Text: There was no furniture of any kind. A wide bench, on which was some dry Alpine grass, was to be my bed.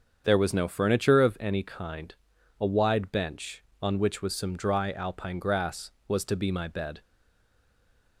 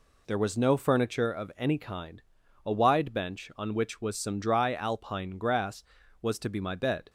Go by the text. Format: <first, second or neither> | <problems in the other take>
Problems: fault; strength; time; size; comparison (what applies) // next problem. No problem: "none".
second | starts louder than the rest; strong; until 1.2 s; 7.5 dB // stays silent after the last word; noticeable; from 7.0 s on; 1.2 s long